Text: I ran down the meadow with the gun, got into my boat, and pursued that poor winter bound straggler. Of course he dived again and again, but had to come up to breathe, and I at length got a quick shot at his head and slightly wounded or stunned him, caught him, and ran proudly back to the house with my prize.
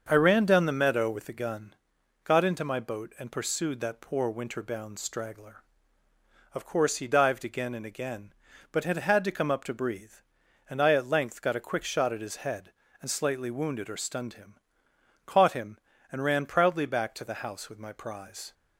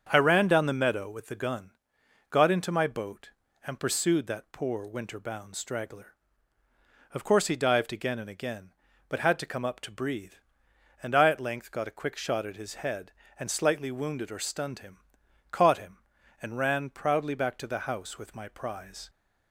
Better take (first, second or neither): second